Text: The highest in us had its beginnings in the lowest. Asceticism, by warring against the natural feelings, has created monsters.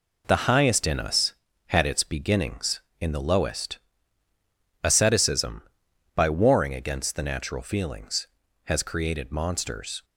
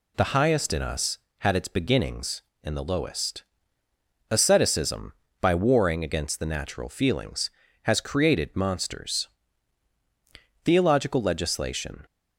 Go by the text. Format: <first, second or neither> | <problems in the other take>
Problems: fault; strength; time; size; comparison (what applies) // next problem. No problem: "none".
first | goes on to say "Theological legislation"; from 10.6 s on; 1.4 s long